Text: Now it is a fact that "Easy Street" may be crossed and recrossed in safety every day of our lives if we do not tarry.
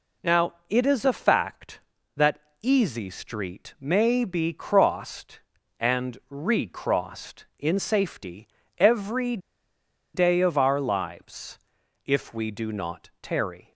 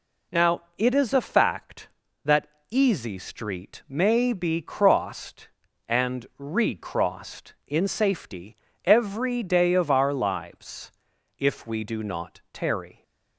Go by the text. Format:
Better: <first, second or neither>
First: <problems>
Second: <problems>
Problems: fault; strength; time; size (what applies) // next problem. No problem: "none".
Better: second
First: pauses between "that" and "Easy"; slight; at 2.3 s; 0.22 s long // pauses between "safety" and "every"; slight; at 8.4 s; 0.30 s long // pauses between "every" and "day"; noticeable; at 9.3 s; 0.80 s long // pauses between "lives" and "if"; noticeable; at 11.5 s; 0.48 s long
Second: pauses between "that" and "Easy"; slight; at 2.4 s; 0.22 s long // pauses between "safety" and "every"; slight; at 8.5 s; 0.28 s long // pauses between "lives" and "if"; noticeable; at 10.9 s; 0.48 s long